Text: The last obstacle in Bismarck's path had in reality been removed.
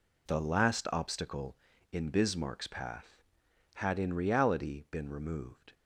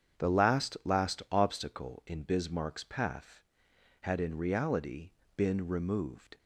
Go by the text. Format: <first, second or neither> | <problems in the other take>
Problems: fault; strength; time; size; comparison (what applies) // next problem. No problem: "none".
first | starts louder than the rest; strong; until 1.3 s; 8 dB // says "last" twice; at 0.8 s // pauses between "reality" and "been"; slight; at 5.0 s; 0.26 s long